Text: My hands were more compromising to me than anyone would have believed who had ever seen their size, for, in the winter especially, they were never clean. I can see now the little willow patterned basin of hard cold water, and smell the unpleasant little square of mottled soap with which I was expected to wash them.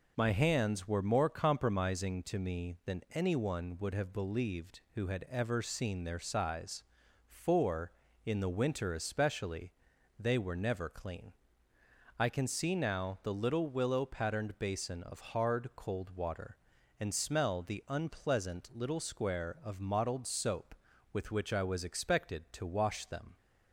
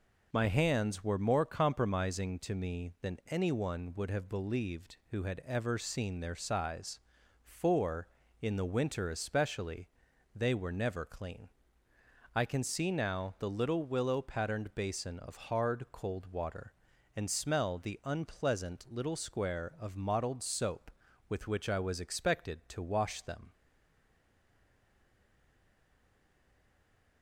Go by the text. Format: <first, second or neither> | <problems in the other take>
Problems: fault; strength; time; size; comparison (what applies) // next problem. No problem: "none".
first | stays silent after the last word; strong; from 23.5 s on; 3.7 s long